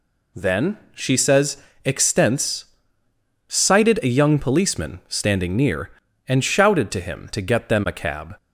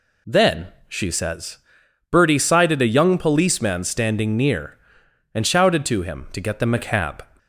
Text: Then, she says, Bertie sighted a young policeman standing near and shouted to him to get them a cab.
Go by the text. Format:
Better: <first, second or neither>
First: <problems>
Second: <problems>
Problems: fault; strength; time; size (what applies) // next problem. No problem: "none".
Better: second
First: says "Extents" for "Bertie"; at 1.8 s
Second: none